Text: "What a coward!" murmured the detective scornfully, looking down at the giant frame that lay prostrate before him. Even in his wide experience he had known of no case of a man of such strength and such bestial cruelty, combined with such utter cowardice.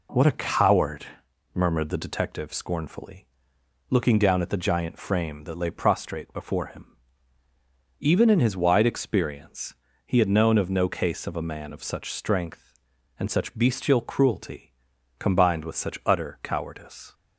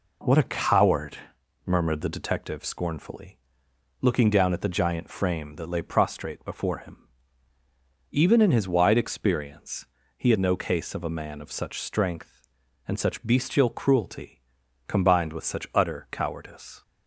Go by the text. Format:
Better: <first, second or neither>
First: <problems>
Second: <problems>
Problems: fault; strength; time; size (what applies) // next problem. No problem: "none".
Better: first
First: pauses between "experience" and "he"; slight; at 9.7 s; 0.30 s long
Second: pauses between "experience" and "he"; slight; at 9.8 s; 0.30 s long // skips "known of"; at 10.3 s